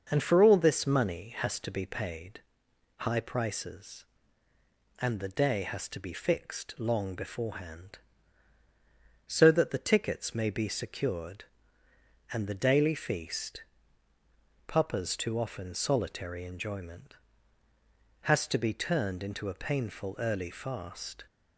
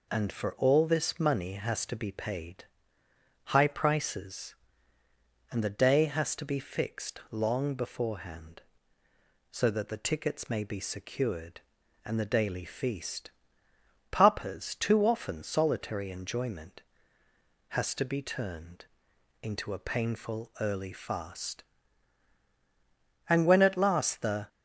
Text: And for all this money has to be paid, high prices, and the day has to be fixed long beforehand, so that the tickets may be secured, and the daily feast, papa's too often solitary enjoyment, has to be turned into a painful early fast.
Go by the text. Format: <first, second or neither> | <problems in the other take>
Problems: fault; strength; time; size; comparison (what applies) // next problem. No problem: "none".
first | pauses between "turned" and "into"; noticeable; at 18.8 s; 0.56 s long // goes on to say "And when at last the"; noticeable; from 23.2 s on; 1.2 s long